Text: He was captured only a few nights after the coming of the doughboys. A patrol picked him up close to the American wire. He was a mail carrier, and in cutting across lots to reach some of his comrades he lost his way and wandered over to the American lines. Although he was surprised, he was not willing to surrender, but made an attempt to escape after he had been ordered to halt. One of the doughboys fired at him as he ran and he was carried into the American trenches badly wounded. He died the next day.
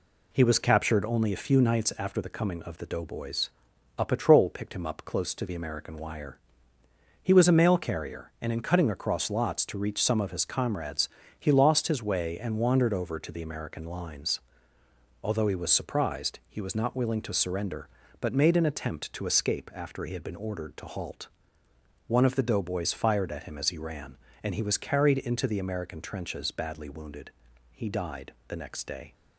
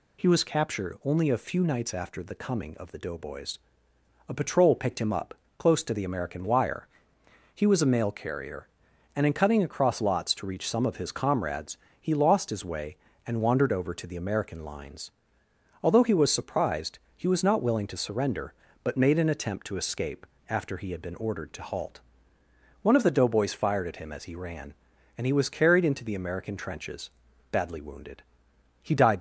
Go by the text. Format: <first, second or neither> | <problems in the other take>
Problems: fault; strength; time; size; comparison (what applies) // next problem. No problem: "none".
first | pauses between "up" and "close"; slight; at 5.3 s; 0.24 s long // pauses between "comrades" and "he"; slight; at 11.7 s; 0.24 s long; slight in the first // pauses between "escape" and "after"; slight; at 20.2 s; 0.24 s long // pauses between "trenches" and "badly"; at 27.0 s; 0.42 s long // stops before "the next day"; at 29.1 s